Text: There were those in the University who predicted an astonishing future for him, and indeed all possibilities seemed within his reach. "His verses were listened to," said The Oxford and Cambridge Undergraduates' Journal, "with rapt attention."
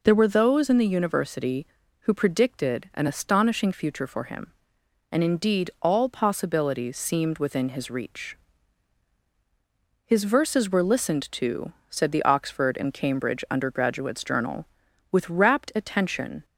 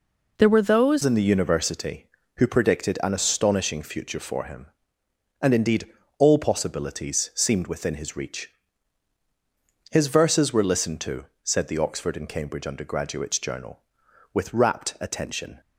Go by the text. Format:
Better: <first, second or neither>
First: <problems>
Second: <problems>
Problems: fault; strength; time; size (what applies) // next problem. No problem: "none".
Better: first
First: none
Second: changes voice at "in"; from 1.0 s on; 14.6 s long // pauses between "indeed" and "all"; slight; at 5.8 s; 0.32 s long